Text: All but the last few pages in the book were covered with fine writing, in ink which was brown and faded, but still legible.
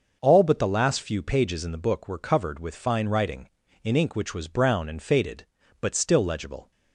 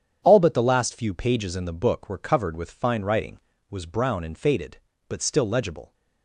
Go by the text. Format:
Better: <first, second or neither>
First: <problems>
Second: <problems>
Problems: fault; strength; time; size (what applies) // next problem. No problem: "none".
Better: first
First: starts louder than the rest; until 1.2 s; 6 dB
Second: starts louder than the rest; strong; until 1.2 s; 8.5 dB // skips "in ink which"; at 3.5 s